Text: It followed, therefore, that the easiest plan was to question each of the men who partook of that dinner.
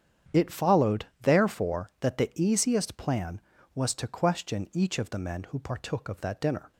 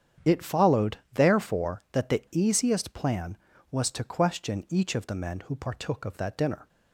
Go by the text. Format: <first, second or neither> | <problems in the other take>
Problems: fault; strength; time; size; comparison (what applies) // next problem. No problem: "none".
neither | starts louder than the rest; strong; the same in both